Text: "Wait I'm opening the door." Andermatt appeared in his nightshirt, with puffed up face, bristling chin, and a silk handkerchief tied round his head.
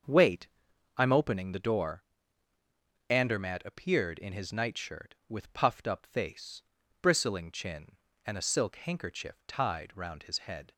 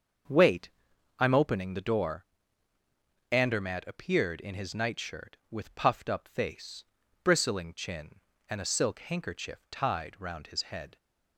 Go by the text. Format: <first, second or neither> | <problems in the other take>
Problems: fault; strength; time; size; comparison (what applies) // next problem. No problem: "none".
neither | starts louder than the rest; the same in both // pauses between "Wait" and "I'm"; noticeable; the same in both